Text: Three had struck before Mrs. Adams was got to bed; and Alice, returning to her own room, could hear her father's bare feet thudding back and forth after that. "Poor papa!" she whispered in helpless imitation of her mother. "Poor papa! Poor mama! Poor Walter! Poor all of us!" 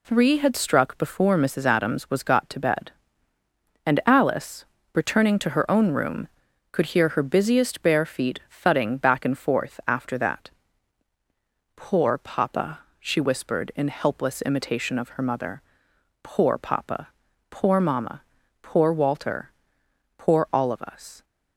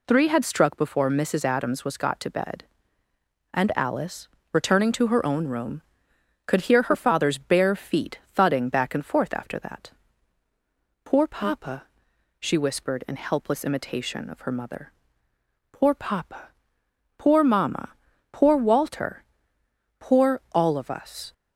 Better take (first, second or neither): second